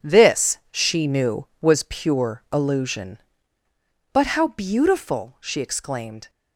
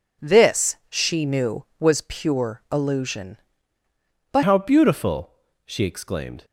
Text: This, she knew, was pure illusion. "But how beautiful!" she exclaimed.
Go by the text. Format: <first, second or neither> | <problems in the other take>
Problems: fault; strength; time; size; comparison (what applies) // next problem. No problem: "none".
first | changes voice at "how"; from 4.4 s on; 2.0 s long